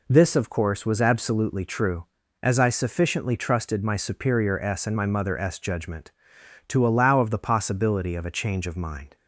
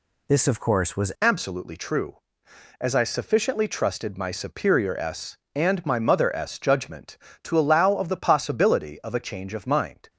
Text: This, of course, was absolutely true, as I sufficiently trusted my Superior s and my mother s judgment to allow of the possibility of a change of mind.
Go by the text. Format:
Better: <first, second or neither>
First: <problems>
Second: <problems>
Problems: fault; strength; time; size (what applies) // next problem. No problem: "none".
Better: first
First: none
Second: changes voice at "absolutely"; from 1.2 s on; 8.8 s long